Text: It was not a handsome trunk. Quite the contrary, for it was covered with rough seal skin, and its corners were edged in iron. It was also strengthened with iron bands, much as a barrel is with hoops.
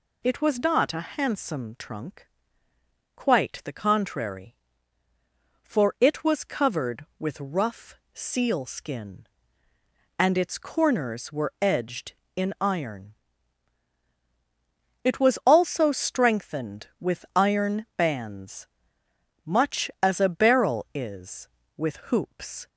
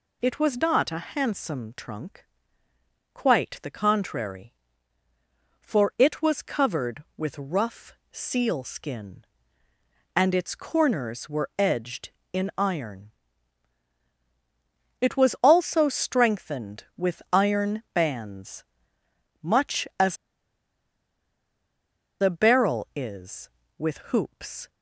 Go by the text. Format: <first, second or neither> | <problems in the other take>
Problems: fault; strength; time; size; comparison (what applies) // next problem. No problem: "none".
first | pauses between "rough" and "seal"; slight; at 7.9 s; 0.20 s long; slight in the first // pauses between "as" and "a"; strong; at 20.1 s; 2.0 s long